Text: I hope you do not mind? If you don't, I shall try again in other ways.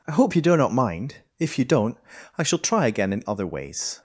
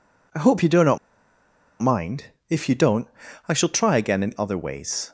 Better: first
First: none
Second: pauses between "not" and "mind"; noticeable; at 0.9 s; 0.83 s long

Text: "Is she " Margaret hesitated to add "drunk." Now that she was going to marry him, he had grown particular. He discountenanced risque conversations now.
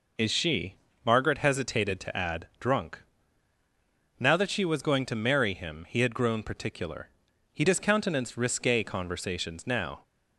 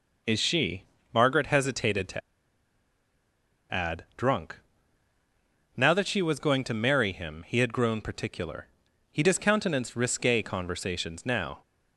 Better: first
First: none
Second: pauses between "to" and "add"; strong; at 2.2 s; 1.5 s long

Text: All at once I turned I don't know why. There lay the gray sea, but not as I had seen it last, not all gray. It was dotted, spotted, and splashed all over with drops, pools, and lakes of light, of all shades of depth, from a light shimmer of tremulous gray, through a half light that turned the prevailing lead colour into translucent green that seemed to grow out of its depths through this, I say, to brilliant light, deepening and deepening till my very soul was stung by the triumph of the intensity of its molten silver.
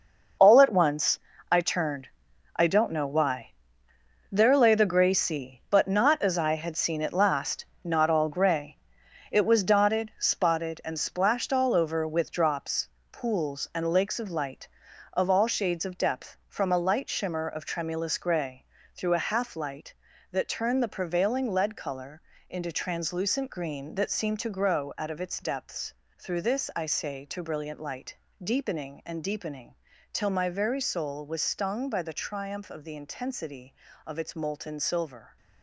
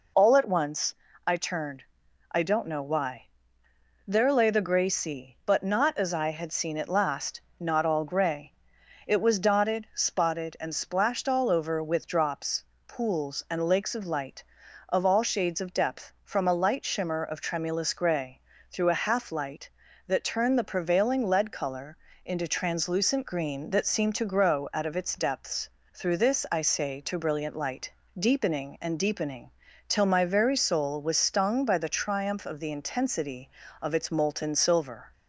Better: second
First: gets quieter; strong; throughout; 10.5 dB // pauses between "once" and "I"; slight; at 1.1 s; 0.32 s long // pauses between "turned" and "I"; noticeable; at 2.0 s; 0.48 s long // pauses between "colour" and "into"; slight; at 22.2 s; 0.28 s long // pauses between "depths" and "through"; slight; at 25.9 s; 0.24 s long // pauses between "deepening" and "till"; slight; at 29.7 s; 0.36 s long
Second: pauses between "once" and "I"; slight; at 0.9 s; 0.32 s long // pauses between "turned" and "I"; noticeable; at 1.8 s; 0.48 s long // pauses between "colour" and "into"; slight; at 21.9 s; 0.28 s long // pauses between "depths" and "through"; slight; at 25.6 s; 0.24 s long // pauses between "deepening" and "till"; slight; at 29.4 s; 0.36 s long

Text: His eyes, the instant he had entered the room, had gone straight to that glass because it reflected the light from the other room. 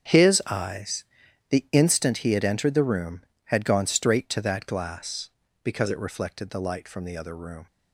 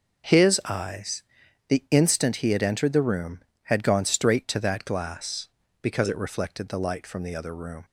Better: second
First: gets quieter; strong; throughout; 14 dB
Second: none

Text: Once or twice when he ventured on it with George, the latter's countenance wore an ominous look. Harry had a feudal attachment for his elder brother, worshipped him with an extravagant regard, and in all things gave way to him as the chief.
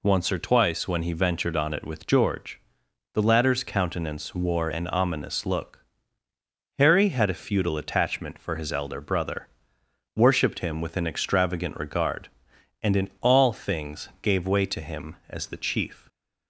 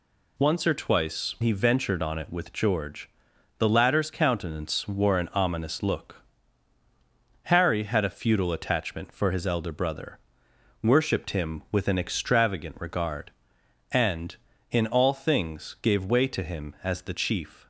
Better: first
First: none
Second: skips "when"; at 1.3 s

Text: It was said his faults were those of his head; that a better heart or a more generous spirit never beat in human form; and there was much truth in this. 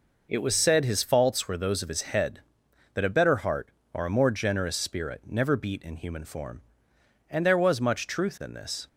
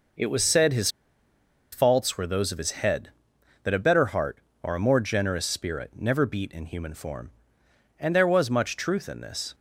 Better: first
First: none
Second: pauses between "his" and "faults"; noticeable; at 0.8 s; 0.83 s long

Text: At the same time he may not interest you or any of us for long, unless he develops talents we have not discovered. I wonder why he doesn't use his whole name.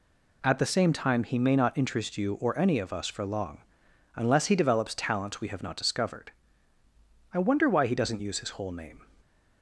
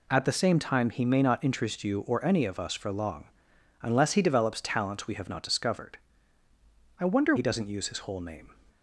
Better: first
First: none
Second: skips "why"; at 7.3 s

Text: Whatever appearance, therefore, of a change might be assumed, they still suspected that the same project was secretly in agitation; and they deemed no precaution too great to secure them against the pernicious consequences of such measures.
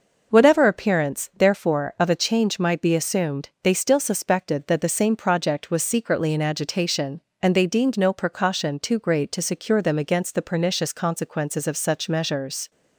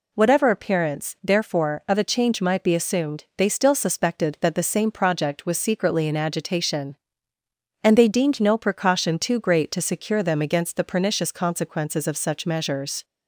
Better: neither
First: none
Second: none

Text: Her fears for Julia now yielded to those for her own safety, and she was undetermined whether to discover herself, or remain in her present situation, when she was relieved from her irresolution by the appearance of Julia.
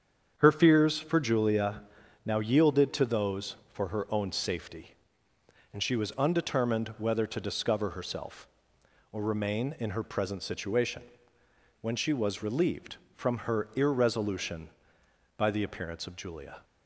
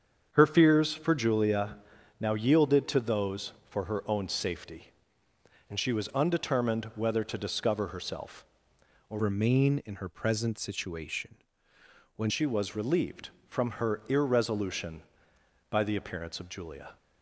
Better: first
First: starts louder than the rest; strong; until 1.3 s; 7.5 dB // pauses between "Julia" and "now"; at 1.8 s; 0.42 s long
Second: starts louder than the rest; strong; until 1.3 s; 7.5 dB // pauses between "Julia" and "now"; at 1.7 s; 0.42 s long // changes voice from "remain" to "when"; from 9.1 to 12.2 s; 3.1 s long

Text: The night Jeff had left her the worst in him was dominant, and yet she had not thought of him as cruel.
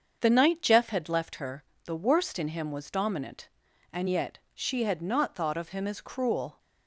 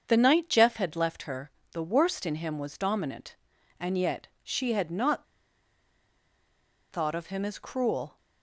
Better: first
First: starts louder than the rest; until 1.2 s; 7 dB // pauses between "her" and "the"; slight; at 1.6 s; 0.22 s long // pauses between "yet" and "she"; slight; at 4.3 s; 0.16 s long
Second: starts louder than the rest; until 1.0 s; 7 dB // pauses between "her" and "the"; slight; at 1.4 s; 0.22 s long // pauses between "yet" and "she"; slight; at 4.2 s; 0.16 s long // pauses between "not" and "thought"; strong; at 5.2 s; 1.6 s long

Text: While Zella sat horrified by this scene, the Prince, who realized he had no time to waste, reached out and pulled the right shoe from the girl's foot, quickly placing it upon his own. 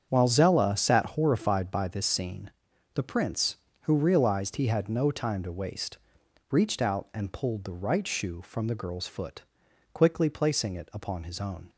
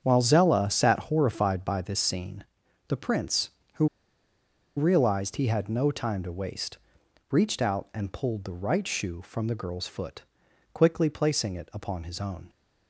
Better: first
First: starts louder than the rest; strong; until 1.1 s; 8 dB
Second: starts louder than the rest; strong; until 1.0 s; 8 dB // pauses between "who" and "realized"; noticeable; at 3.8 s; 0.91 s long

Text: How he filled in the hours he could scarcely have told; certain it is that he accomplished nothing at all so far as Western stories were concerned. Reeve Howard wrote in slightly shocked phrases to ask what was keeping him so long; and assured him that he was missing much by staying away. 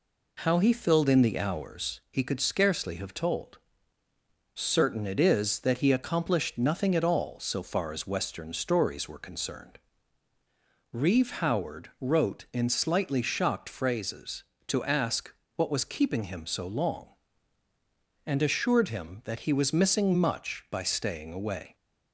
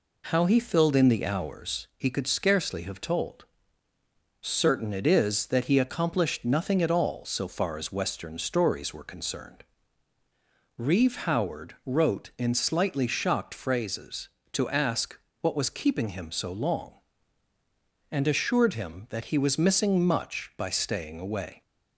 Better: neither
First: pauses between "ask" and "what"; slight; at 15.3 s; 0.22 s long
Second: pauses between "ask" and "what"; slight; at 15.1 s; 0.22 s long

